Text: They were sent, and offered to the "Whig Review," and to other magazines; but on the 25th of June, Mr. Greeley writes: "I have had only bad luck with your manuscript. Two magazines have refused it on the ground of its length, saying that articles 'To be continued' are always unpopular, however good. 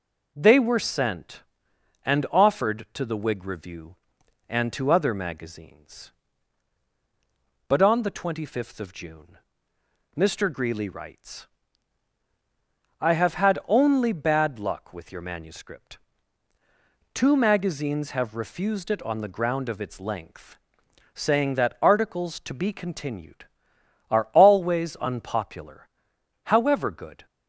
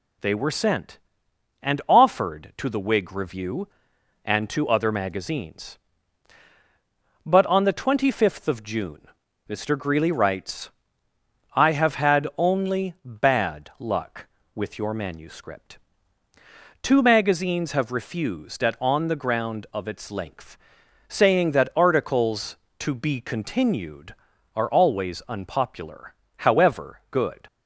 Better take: first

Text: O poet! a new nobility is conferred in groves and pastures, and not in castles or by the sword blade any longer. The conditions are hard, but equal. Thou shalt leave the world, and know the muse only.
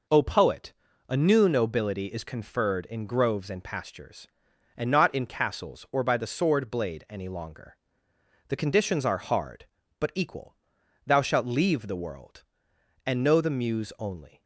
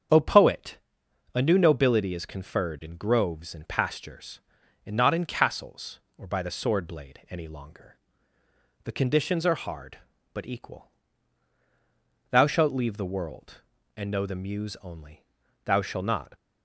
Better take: first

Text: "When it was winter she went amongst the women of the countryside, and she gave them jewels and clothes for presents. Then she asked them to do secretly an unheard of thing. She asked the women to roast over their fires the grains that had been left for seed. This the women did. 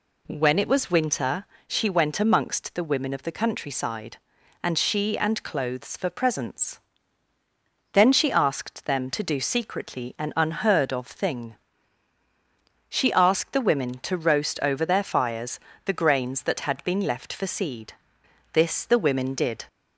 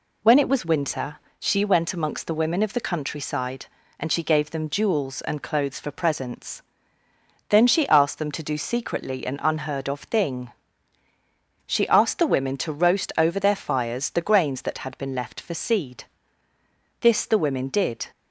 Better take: second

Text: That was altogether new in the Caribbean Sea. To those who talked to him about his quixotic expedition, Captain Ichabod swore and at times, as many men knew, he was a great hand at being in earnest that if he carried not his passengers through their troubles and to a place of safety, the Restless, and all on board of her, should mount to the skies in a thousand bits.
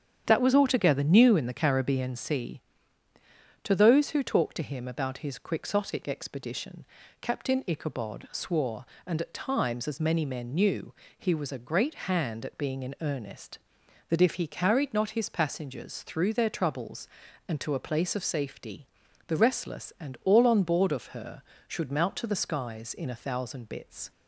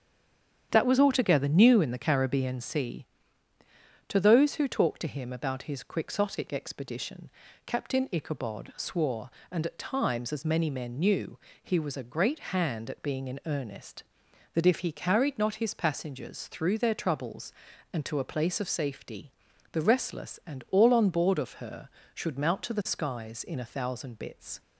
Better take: first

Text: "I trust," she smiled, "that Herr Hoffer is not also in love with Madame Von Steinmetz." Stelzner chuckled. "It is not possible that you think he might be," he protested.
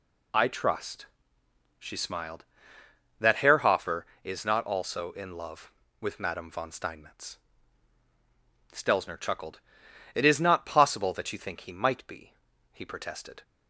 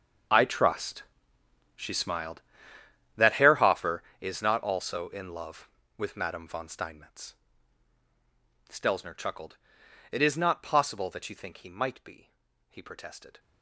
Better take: first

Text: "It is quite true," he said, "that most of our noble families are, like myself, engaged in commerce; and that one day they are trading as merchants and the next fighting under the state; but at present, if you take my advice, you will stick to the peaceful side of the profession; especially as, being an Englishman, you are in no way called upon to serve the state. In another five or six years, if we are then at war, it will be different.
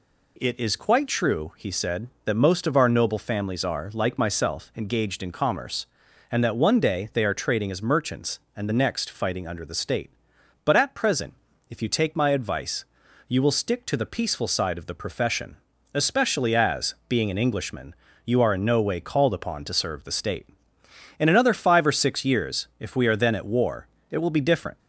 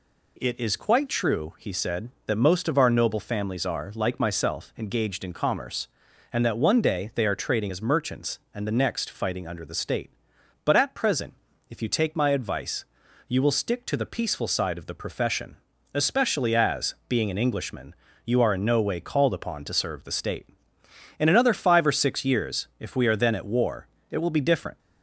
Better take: neither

